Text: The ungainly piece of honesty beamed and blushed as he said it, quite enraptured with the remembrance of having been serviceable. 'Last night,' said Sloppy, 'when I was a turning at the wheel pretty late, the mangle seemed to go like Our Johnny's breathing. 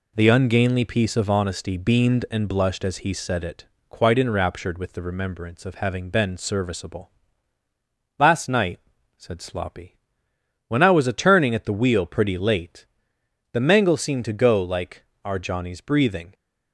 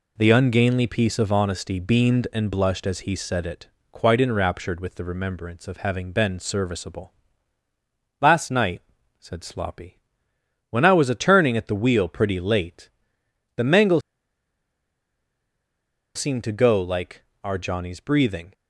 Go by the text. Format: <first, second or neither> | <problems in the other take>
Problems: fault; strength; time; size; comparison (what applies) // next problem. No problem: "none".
first | pauses between "mangle" and "seemed"; strong; at 14.0 s; 2.1 s long // pauses between "like" and "Our"; slight; at 17.2 s; 0.20 s long; slight in the first